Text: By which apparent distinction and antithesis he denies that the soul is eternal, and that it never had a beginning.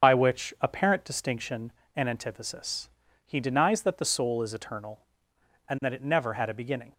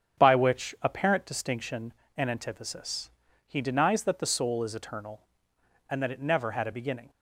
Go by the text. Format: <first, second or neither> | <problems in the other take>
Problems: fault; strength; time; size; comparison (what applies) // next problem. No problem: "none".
second | loses the start of "By"; at 0.0 s; 50 ms // starts louder than the rest; strong; until 1.1 s; 7 dB; strong in the second // pauses between "antithesis" and "he"; at 2.8 s; 0.38 s long; also in the second